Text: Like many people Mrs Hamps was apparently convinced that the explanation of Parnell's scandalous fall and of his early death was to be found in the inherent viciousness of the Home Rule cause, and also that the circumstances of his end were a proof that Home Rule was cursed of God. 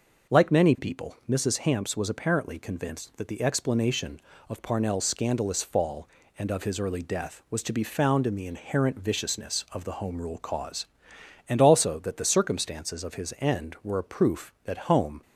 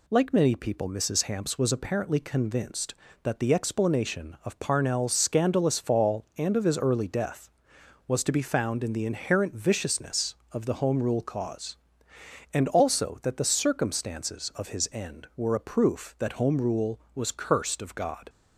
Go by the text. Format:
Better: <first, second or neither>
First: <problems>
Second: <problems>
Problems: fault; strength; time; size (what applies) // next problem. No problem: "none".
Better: second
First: stops before "Rule was cursed of God"; at 15.2 s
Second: none